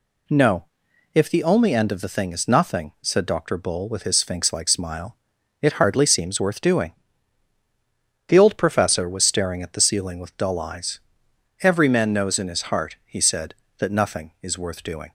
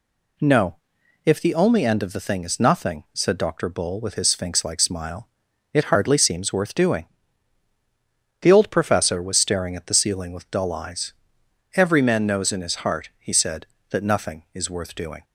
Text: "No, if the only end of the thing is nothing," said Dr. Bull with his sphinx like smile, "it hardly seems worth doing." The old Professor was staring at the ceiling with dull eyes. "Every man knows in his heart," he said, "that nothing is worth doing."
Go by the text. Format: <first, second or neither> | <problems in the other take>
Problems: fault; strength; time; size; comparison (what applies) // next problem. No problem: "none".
neither | none